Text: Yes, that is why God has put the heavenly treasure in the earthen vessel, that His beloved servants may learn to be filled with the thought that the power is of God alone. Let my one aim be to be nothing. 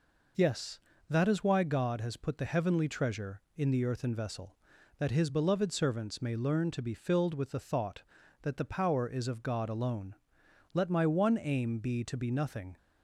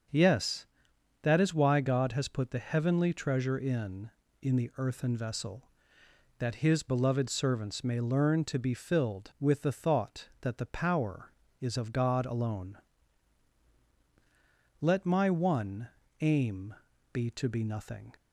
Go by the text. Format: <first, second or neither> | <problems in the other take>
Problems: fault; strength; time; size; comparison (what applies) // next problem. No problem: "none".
first | starts louder than the rest; strong; until 1.6 s; 7 dB // says "in" twice; at 4.4 s // pauses between "one" and "aim"; slight; at 15.8 s; 0.32 s long // pauses between "aim" and "be"; at 16.7 s; 0.38 s long